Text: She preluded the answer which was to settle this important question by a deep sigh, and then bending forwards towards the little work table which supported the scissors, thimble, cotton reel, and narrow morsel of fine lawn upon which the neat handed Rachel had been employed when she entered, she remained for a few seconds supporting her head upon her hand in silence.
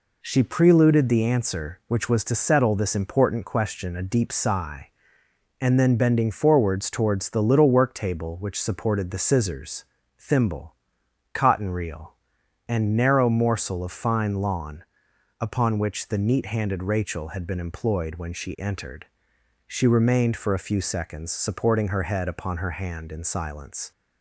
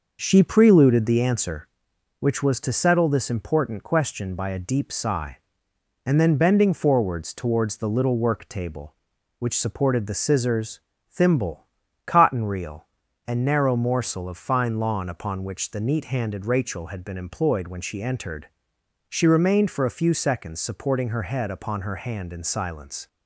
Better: second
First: skips "by"; at 3.9 s // pauses between "lawn" and "upon"; noticeable; at 14.8 s; 0.56 s long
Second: none

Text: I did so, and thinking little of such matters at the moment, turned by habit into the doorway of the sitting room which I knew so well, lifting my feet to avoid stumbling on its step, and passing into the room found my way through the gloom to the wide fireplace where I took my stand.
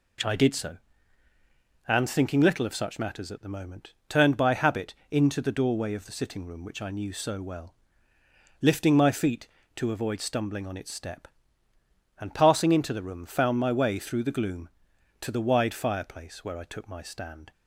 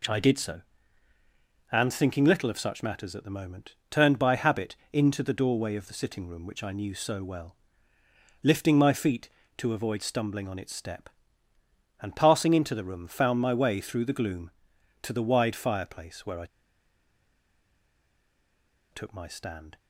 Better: first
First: pauses between "habit" and "into"; slight; at 4.9 s; 0.16 s long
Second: pauses between "habit" and "into"; slight; at 4.7 s; 0.16 s long // pauses between "I" and "took"; strong; at 16.4 s; 2.4 s long

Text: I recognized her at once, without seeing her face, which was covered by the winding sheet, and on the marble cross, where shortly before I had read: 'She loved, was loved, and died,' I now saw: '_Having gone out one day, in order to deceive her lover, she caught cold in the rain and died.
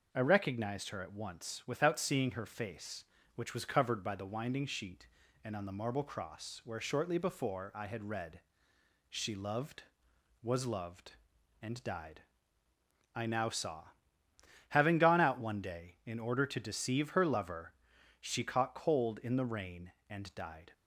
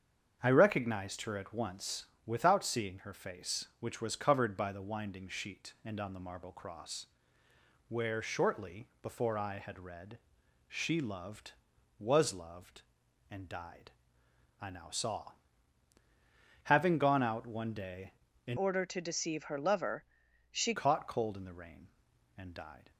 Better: first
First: none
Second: starts louder than the rest; strong; until 1.4 s; 7.5 dB // changes voice from "order" to "she"; from 18.5 to 20.7 s; 2.2 s long

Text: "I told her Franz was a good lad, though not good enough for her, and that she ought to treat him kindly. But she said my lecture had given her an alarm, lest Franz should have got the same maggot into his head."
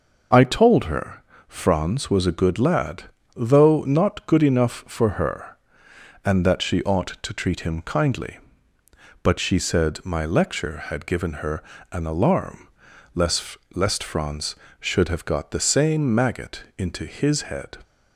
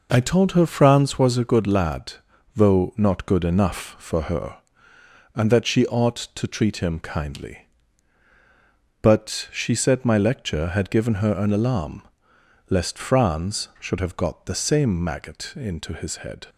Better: second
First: pauses between "her" and "Franz"; slight; at 1.2 s; 0.24 s long // pauses between "her" and "an"; slight; at 11.6 s; 0.30 s long // says "lest" twice; at 13.7 s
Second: none

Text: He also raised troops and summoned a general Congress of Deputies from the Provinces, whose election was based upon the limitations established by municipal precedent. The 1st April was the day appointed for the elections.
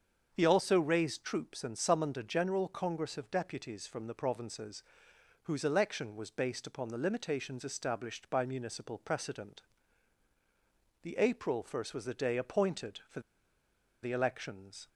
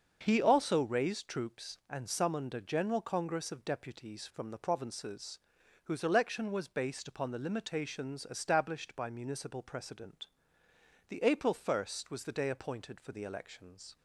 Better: second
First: starts louder than the rest; until 1.3 s; 7 dB // pauses between "for" and "the"; noticeable; at 13.1 s; 0.83 s long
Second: starts louder than the rest; until 1.2 s; 6.5 dB

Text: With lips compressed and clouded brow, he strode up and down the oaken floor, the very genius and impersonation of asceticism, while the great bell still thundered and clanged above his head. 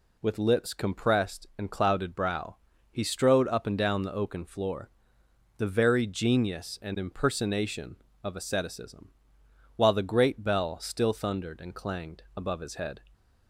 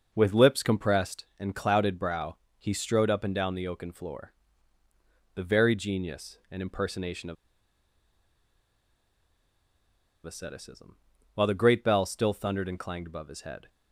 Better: first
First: none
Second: pauses between "of" and "asceticism"; strong; at 7.3 s; 2.9 s long

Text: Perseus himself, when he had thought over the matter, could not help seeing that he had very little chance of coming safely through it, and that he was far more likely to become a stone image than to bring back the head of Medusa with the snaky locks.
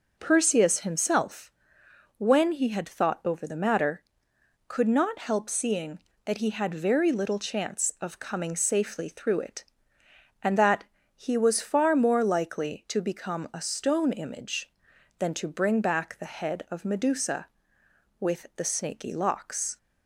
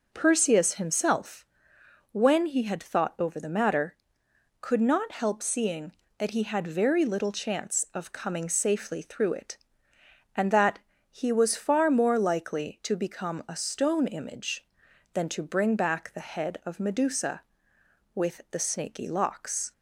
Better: neither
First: pauses between "that" and "he"; slight; at 10.8 s; 0.30 s long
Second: pauses between "that" and "he"; slight; at 10.8 s; 0.30 s long

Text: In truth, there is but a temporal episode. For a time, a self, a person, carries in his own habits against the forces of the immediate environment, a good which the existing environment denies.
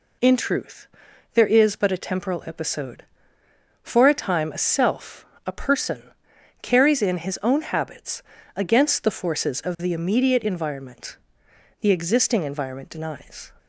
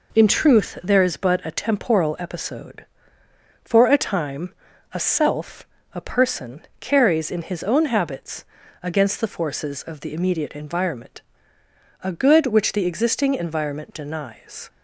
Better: second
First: pauses between "habits" and "against"; slight; at 8.2 s; 0.34 s long // skips "a good which"; at 11.4 s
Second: pauses between "habits" and "against"; at 8.4 s; 0.38 s long

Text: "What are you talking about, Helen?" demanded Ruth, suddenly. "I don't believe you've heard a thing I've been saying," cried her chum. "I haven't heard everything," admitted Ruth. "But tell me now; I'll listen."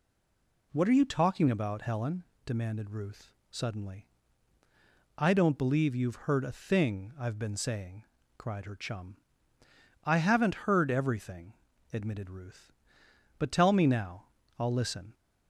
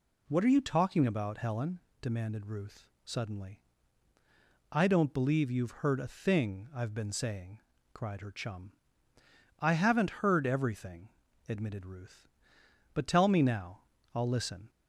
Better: second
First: stays silent before the first word; slight; until 0.7 s; 0.7 s long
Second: none

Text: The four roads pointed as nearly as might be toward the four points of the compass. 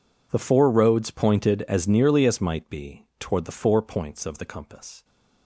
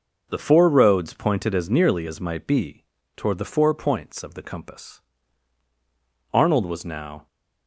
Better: first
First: none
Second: pauses between "be" and "toward"; slight; at 2.8 s; 0.32 s long // goes on to say "Arnold was now"; noticeable; from 6.3 s on; 0.94 s long

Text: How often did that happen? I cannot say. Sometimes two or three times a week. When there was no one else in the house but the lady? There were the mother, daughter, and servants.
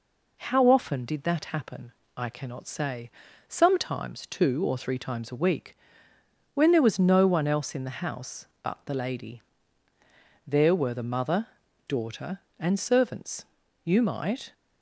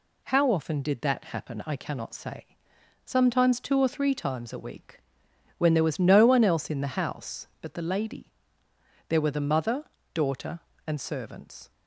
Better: second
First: goes on to say "You might"; noticeable; from 13.8 s on; 0.70 s long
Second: none

